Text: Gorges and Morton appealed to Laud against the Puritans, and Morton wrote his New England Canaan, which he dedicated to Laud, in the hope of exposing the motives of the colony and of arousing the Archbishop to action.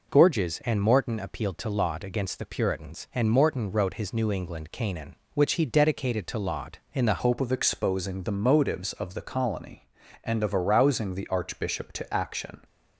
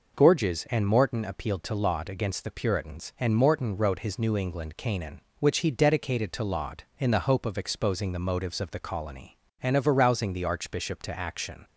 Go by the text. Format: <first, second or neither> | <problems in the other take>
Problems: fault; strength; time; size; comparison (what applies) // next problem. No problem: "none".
second | changes voice at "hope"; from 7.1 s on; 5.4 s long